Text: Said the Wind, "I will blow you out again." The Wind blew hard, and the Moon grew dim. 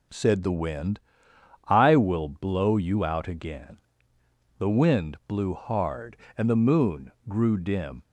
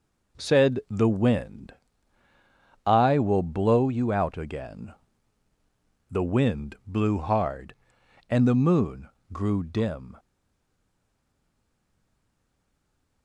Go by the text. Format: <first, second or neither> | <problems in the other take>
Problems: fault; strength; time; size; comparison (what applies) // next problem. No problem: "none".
first | pauses between "Moon" and "grew"; slight; at 9.0 s; 0.24 s long; slight in the first // stays silent after the last word; strong; from 10.1 s on; 3.1 s long